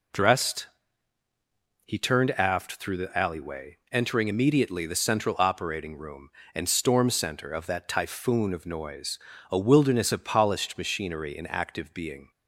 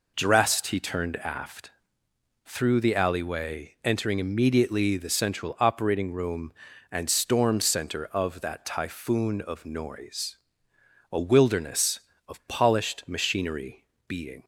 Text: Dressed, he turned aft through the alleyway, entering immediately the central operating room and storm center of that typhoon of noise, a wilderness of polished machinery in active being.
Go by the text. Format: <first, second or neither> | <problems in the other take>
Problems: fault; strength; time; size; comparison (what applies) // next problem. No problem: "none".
first | pauses between "aft" and "through"; noticeable; at 1.6 s; 0.76 s long // skips "in active"; at 13.9 s